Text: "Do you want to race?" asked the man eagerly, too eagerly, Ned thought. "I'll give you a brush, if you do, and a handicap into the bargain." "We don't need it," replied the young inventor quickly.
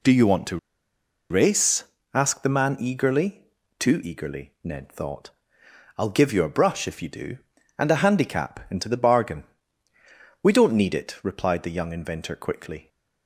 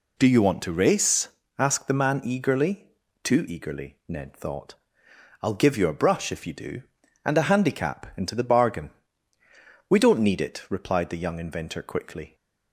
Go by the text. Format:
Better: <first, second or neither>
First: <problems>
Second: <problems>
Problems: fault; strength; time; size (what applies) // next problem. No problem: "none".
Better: second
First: pauses between "to" and "race"; noticeable; at 0.5 s; 0.72 s long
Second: none